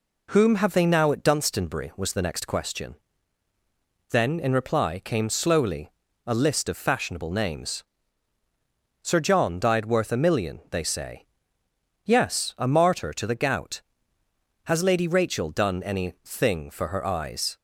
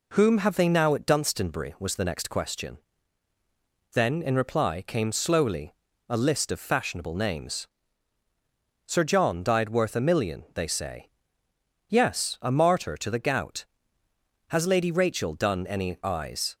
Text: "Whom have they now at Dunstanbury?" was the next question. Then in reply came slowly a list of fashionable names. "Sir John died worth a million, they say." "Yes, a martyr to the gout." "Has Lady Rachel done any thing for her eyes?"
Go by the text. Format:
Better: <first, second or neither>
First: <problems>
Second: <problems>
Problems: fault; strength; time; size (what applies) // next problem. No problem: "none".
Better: first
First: pauses between "slowly" and "a"; at 5.8 s; 0.38 s long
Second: pauses between "slowly" and "a"; at 5.7 s; 0.38 s long // skips "thing for her"; at 16.0 s